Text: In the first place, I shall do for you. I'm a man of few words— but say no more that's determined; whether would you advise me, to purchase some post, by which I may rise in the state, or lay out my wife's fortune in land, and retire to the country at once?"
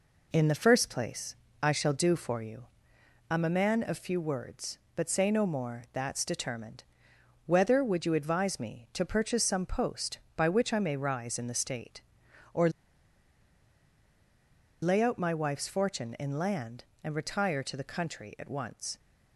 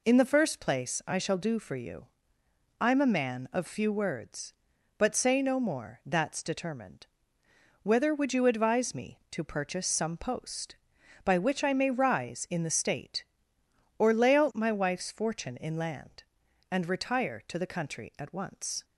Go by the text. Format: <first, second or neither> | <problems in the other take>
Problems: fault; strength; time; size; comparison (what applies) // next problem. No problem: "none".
second | pauses between "or" and "lay"; strong; at 12.6 s; 2.1 s long